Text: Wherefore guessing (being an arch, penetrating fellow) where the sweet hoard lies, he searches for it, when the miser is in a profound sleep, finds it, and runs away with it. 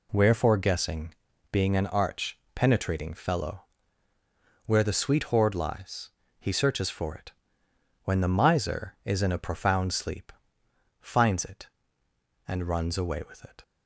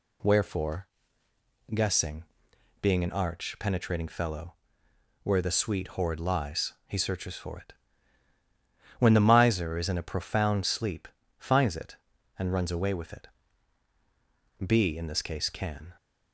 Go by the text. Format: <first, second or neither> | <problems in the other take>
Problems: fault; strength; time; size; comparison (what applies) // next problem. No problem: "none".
first | pauses between "Wherefore" and "guessing"; noticeable; at 0.8 s; 0.88 s long // goes on to say "B in this case can"; noticeable; from 14.6 s on; 1.3 s long